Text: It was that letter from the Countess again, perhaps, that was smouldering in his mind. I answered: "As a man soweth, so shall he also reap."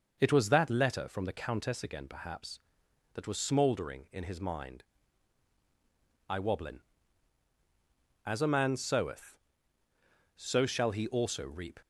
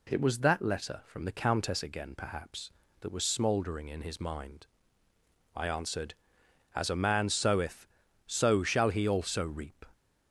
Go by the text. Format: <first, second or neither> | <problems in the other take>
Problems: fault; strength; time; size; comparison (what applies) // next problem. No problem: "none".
second | says "wobblin" for "answered"; at 6.3 s